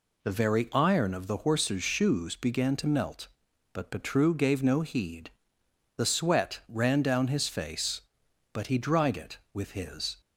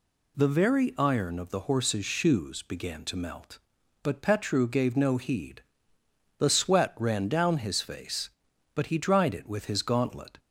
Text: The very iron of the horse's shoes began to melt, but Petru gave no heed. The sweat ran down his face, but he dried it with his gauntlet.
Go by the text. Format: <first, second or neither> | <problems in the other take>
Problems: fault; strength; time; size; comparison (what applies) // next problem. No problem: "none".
second | stops before "gauntlet"; at 10.2 s